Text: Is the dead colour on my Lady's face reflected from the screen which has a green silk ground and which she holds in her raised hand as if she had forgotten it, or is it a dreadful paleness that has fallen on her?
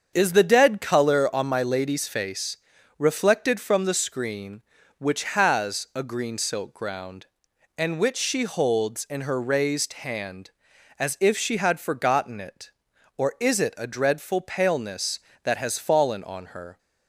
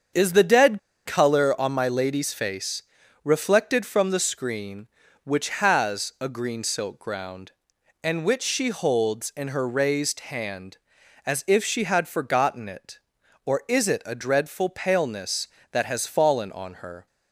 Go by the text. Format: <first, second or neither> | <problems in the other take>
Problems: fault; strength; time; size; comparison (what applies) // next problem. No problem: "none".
first | starts louder than the rest; strong; until 1.4 s; 7 dB; strong in the first // pauses between "dead" and "colour"; slight; at 0.7 s; 0.26 s long // pauses between "face" and "reflected"; at 2.8 s; 0.44 s long; also in the first